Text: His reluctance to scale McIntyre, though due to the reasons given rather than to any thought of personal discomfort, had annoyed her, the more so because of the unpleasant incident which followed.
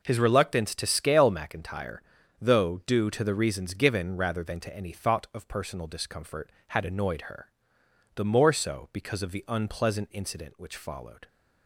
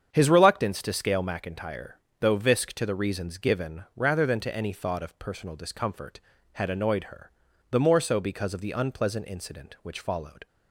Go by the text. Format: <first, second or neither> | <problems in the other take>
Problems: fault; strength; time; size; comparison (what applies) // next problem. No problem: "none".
first | starts louder than the rest; strong; until 1.1 s; 8 dB // says "visk" for "due"; at 2.3 s